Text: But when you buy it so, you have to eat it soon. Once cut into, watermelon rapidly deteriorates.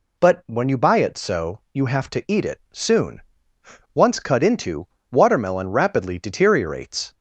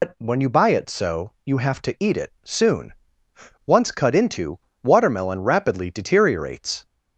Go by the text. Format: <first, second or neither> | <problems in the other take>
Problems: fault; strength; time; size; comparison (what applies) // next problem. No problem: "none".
first | loses the start of "But"; at 0.0 s; 105 ms